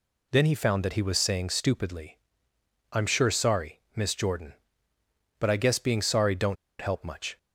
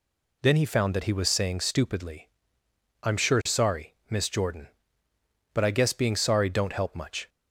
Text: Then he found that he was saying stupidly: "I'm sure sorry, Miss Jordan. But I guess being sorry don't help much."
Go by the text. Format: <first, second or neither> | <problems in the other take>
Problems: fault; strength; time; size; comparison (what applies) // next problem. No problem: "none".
second | pauses between "don't" and "help"; slight; at 6.5 s; 0.25 s long